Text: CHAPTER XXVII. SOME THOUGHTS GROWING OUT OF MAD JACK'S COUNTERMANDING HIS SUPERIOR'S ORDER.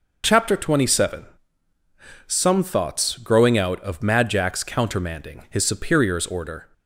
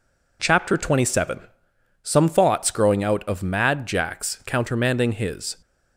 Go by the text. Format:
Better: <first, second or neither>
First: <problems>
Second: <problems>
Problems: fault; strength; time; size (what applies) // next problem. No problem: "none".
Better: first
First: none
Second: stops before "SUPERIOR'S ORDER"; at 5.6 s